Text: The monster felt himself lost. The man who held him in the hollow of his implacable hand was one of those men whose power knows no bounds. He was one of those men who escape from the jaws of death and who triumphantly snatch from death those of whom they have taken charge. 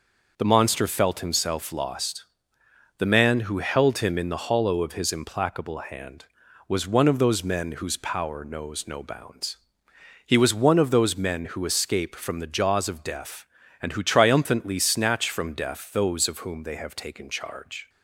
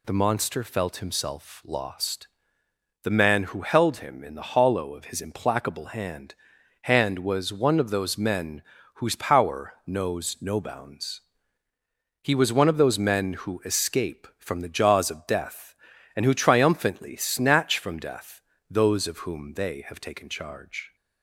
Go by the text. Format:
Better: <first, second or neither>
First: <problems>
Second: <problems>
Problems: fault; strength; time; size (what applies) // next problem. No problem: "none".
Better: first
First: none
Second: says "hand" twice; at 6.8 s // pauses between "men" and "whose"; slight; at 8.6 s; 0.34 s long // pauses between "death" and "those"; slight; at 18.4 s; 0.28 s long